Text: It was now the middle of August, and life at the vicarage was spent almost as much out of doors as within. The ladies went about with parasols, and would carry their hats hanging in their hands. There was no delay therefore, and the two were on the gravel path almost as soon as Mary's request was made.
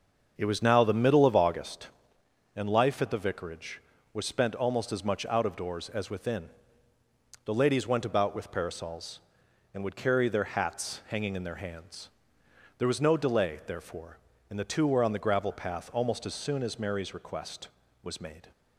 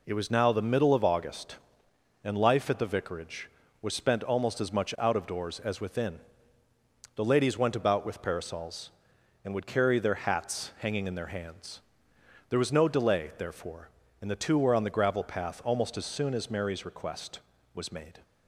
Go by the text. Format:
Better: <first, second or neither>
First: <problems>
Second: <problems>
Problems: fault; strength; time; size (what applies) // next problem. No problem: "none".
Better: second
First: starts louder than the rest; until 1.8 s; 6.5 dB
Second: none